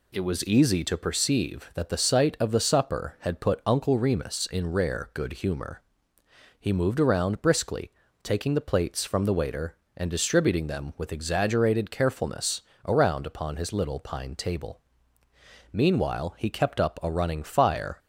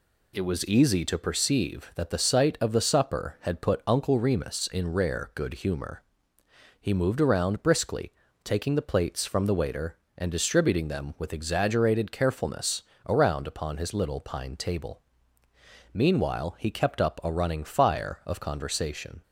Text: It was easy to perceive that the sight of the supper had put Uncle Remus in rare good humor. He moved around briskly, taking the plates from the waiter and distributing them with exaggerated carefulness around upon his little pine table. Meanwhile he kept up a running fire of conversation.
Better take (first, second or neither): second